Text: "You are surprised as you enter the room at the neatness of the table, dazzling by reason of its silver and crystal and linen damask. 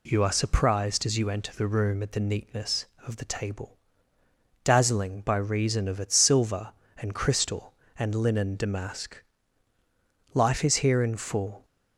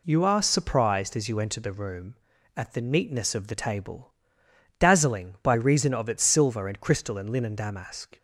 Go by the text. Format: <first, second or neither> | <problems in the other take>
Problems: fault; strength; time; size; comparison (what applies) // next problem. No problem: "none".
second | goes on to say "Life is here in full"; noticeable; from 10.3 s on; 1.3 s long